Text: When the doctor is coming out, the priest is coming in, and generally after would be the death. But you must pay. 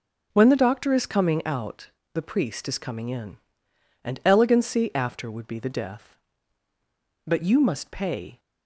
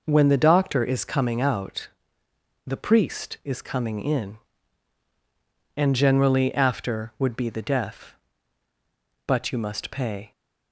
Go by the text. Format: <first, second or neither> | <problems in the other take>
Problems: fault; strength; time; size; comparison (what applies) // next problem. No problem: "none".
second | says "elegancy" for "generally"; at 4.2 s